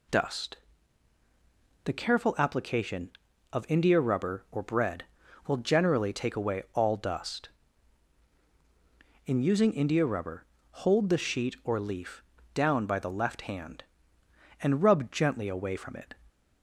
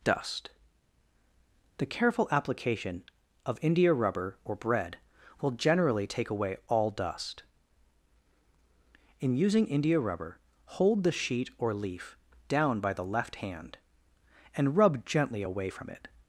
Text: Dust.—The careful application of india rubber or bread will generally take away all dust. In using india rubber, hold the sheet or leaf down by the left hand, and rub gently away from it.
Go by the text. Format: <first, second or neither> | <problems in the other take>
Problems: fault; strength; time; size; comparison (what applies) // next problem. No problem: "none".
neither | pauses between "leaf" and "down"; slight; the same in both